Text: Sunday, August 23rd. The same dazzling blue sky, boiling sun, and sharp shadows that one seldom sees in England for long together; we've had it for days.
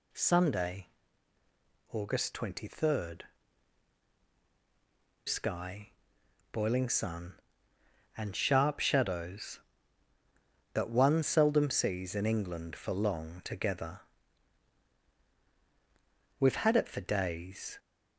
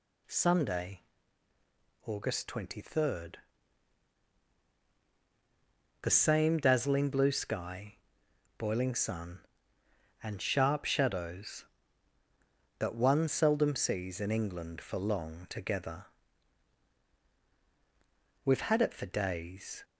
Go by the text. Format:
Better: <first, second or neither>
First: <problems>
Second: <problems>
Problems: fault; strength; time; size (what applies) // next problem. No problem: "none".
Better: second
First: skips "The same dazzling blue"; at 4.2 s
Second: none